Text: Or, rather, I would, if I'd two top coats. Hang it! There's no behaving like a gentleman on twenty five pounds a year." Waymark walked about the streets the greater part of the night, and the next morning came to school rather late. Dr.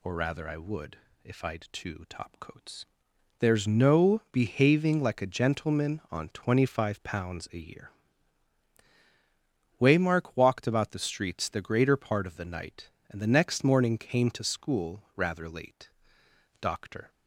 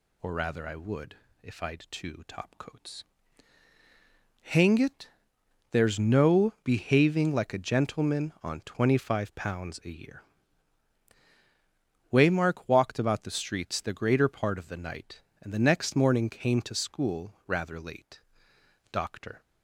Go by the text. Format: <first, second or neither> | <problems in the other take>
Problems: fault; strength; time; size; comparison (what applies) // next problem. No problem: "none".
second | skips "Hang it"; at 3.1 s